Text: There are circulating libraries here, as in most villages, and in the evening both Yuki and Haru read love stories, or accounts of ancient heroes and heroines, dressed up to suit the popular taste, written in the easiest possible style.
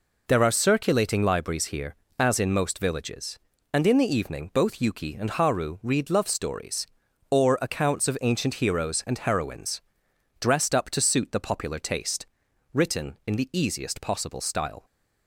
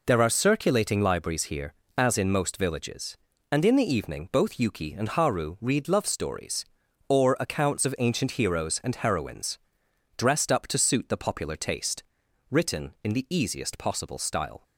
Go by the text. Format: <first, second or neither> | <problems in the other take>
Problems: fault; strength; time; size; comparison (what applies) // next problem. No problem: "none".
neither | none